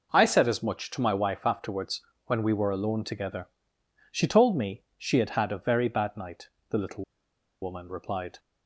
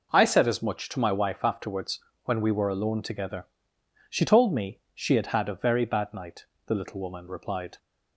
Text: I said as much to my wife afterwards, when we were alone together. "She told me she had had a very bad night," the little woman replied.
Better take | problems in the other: second | pauses between "me" and "she"; slight; at 4.8 s; 0.16 s long; slight in the second // pauses between "little" and "woman"; noticeable; at 7.0 s; 0.58 s long

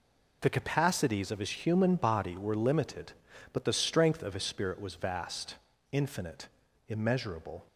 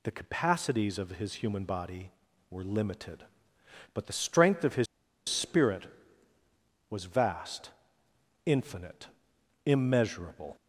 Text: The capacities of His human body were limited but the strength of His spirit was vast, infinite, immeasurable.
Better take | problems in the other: first | pauses between "His" and "spirit"; at 4.8 s; 0.43 s long

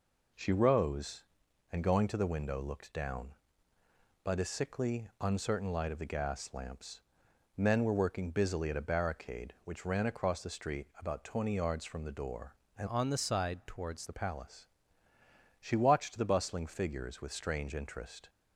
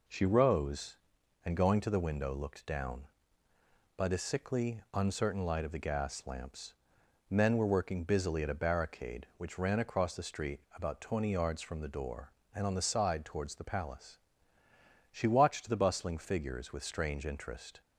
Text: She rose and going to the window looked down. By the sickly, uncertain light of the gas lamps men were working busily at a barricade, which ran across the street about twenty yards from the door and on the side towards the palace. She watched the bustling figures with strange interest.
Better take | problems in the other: second | pauses between "lamps" and "men"; noticeable; at 7.0 s; 0.54 s long; noticeable in the second // changes voice from "on" to "towards"; from 12.8 to 14.0 s; 1.2 s long

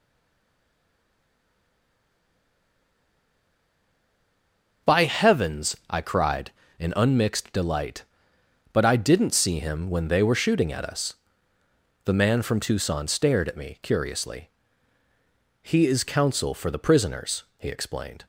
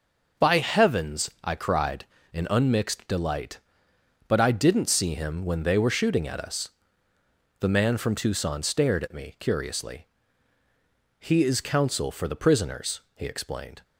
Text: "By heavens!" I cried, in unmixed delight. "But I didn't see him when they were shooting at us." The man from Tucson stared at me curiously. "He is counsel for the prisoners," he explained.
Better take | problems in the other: second | stays silent before the first word; strong; until 4.8 s; 4.8 s long

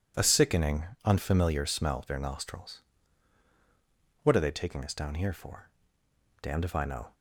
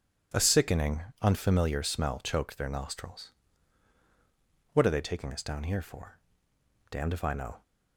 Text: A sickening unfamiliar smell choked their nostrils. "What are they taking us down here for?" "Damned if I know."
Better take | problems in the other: second | pauses between "sickening" and "unfamiliar"; slight; at 0.8 s; 0.18 s long; slight in the second // skips "choked"; at 2.0 s

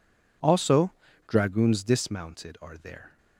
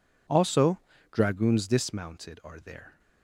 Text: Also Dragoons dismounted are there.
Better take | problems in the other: neither | pauses between "Also" and "Dragoons"; slight; the same in both

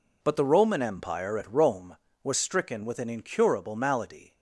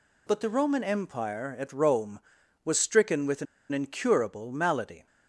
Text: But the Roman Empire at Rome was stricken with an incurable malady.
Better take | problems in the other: first | pauses between "an" and "incurable"; slight; at 3.4 s; 0.26 s long

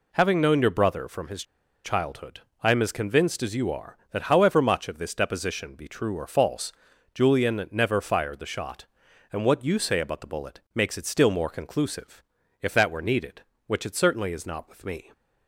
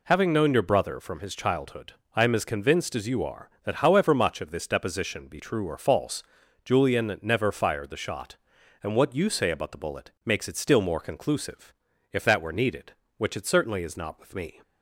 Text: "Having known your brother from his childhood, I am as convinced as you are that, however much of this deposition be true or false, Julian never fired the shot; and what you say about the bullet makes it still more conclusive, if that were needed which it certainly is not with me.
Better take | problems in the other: second | pauses between "his" and "childhood"; at 1.4 s; 0.40 s long

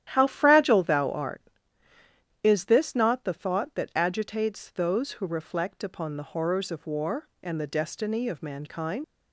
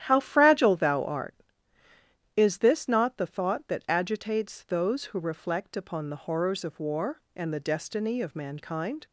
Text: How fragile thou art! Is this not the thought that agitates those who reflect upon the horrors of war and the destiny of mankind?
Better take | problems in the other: second | starts louder than the rest; strong; until 1.1 s; 11.5 dB; strong in the second // leaves "mankind" unfinished; at 9.0 s; 80 ms

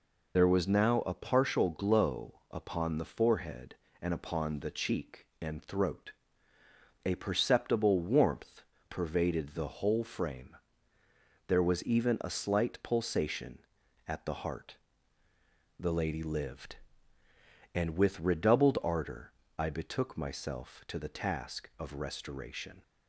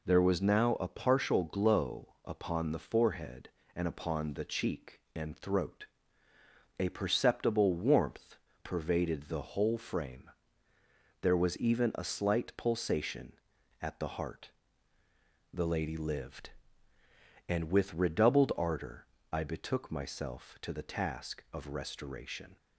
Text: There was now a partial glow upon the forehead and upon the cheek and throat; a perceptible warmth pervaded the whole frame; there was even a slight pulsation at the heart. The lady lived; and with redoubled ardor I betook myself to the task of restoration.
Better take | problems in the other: second | loses the start of "There"; at 0.3 s; 50 ms // pauses between "warmth" and "pervaded"; slight; at 8.6 s; 0.28 s long; slight in the second // pauses between "ardor" and "I"; slight; at 19.3 s; 0.26 s long; slight in the second

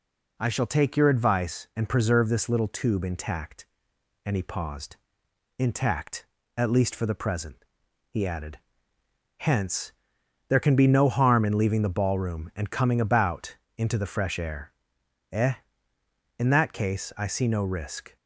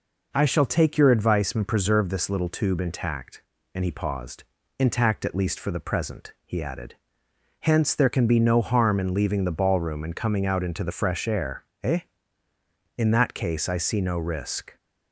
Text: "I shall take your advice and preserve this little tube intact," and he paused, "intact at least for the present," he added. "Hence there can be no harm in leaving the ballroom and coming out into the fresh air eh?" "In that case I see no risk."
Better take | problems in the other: second | pauses between "Hence" and "there"; noticeable; at 9.9 s; 0.58 s long // says "about" for "out"; at 12.9 s // pauses between "air" and "eh"; noticeable; at 14.7 s; 0.58 s long; slight in the second

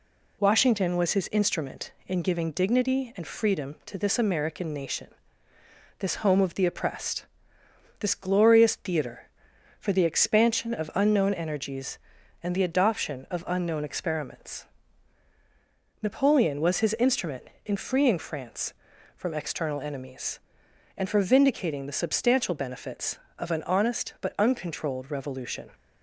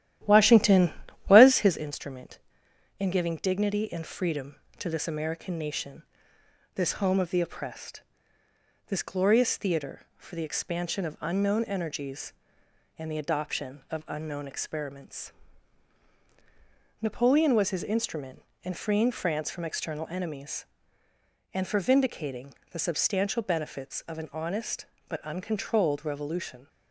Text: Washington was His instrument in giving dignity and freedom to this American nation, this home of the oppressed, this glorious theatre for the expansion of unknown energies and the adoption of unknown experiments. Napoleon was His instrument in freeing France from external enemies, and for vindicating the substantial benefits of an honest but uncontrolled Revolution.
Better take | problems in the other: first | starts louder than the rest; strong; until 1.8 s; 12.5 dB // pauses between "vindicating" and "the"; slight; at 22.5 s; 0.16 s long

